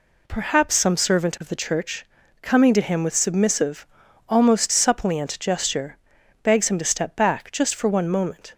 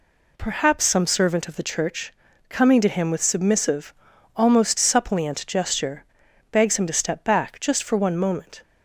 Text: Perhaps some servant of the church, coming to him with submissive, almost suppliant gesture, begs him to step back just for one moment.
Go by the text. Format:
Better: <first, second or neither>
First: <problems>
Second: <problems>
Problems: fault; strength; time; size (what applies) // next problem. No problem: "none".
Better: neither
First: none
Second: none